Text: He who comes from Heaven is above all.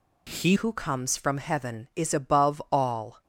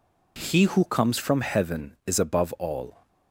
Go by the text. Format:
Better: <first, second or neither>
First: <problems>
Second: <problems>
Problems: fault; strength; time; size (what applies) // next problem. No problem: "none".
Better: second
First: changes voice at "who"; from 0.5 s on; 2.7 s long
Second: none